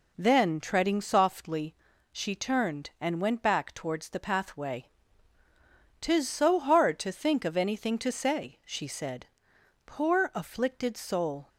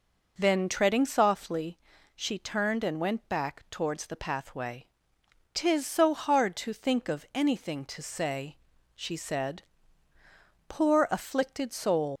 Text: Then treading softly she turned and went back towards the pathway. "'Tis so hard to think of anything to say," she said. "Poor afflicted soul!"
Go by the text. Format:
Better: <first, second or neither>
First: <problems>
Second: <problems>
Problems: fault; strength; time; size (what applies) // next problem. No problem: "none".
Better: first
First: pauses between "softly" and "she"; at 1.7 s; 0.38 s long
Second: pauses between "softly" and "she"; slight; at 1.7 s; 0.36 s long // leaves "soul" unfinished; at 12.1 s; 110 ms